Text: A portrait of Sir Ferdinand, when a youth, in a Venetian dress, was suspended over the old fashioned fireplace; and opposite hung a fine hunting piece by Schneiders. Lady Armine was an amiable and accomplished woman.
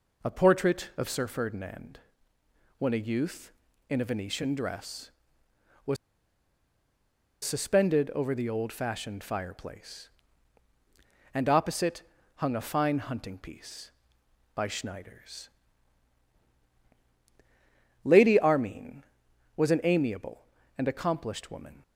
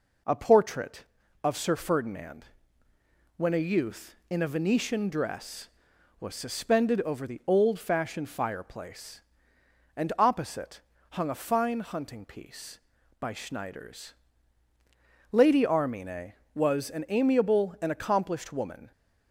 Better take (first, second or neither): second